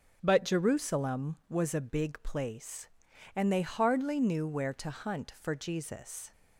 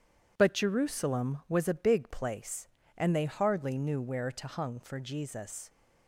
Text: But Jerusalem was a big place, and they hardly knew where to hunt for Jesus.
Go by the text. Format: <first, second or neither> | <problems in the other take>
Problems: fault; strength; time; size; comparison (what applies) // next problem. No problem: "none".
first | says "hung" for "hunt"; at 4.4 s